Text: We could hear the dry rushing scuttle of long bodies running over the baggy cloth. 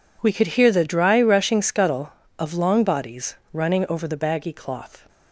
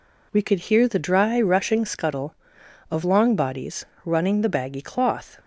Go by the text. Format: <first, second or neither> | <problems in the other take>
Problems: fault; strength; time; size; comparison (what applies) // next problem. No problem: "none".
first | pauses between "bodies" and "running"; slight; at 3.8 s; 0.18 s long; slight in the first // skips "over"; at 4.4 s